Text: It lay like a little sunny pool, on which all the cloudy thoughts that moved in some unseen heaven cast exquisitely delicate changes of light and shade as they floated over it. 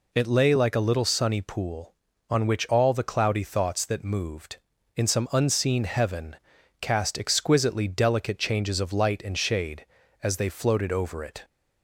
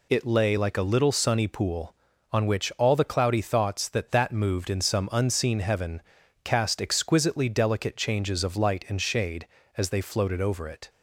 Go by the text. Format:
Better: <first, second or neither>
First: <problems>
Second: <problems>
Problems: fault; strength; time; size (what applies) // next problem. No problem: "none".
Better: first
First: pauses between "heaven" and "cast"; noticeable; at 6.3 s; 0.46 s long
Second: says "that" twice; at 4.1 s // pauses between "heaven" and "cast"; at 6.0 s; 0.42 s long